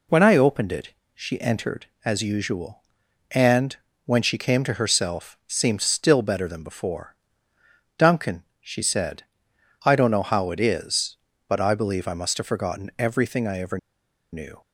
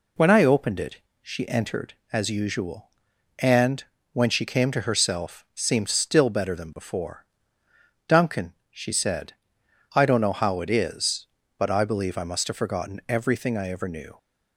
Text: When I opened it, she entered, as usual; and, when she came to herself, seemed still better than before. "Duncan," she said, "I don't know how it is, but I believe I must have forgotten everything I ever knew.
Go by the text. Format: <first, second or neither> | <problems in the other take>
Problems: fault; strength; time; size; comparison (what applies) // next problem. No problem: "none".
second | pauses between "ever" and "knew"; noticeable; at 13.7 s; 0.54 s long